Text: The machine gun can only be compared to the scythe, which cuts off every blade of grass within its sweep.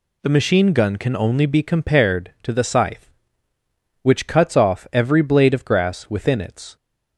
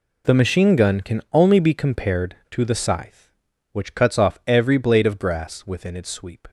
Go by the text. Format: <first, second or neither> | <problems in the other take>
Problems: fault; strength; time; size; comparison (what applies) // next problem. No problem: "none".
second | stops before "sweep"; at 6.7 s